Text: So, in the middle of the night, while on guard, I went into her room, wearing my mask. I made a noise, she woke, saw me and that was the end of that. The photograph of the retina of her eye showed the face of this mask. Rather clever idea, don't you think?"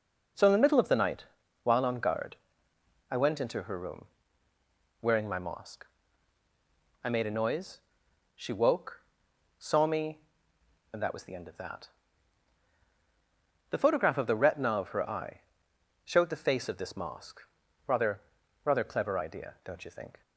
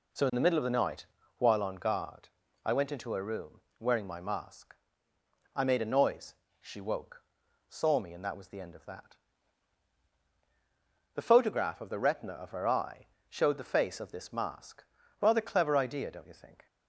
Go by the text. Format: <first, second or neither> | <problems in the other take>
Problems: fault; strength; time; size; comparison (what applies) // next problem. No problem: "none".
second | pauses between "eye" and "showed"; noticeable; at 15.4 s; 0.64 s long; slight in the second // says "Rather" twice; at 18.6 s